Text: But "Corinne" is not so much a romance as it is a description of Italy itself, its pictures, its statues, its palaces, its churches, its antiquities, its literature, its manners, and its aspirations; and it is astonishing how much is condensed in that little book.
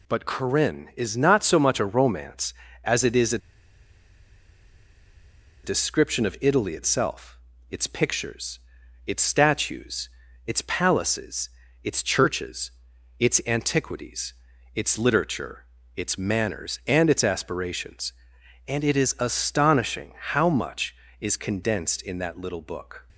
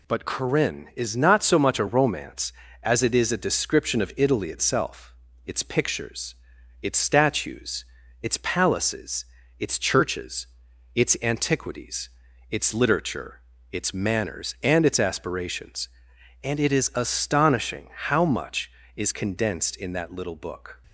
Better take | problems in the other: second | pauses between "a" and "description"; strong; at 3.3 s; 2.2 s long

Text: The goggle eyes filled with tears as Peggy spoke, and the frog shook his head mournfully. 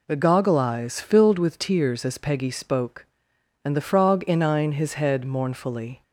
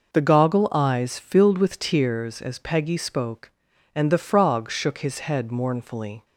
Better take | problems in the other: second | says "inine" for "shook"; at 4.2 s

